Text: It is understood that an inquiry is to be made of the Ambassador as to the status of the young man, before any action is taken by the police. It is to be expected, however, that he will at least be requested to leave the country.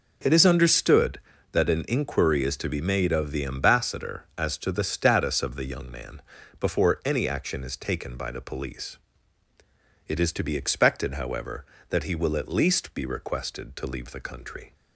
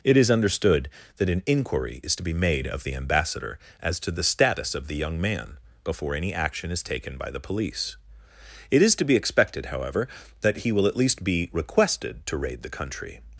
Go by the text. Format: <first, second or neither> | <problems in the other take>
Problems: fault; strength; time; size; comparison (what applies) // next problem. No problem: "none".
first | says "raid" for "leave"; at 12.3 s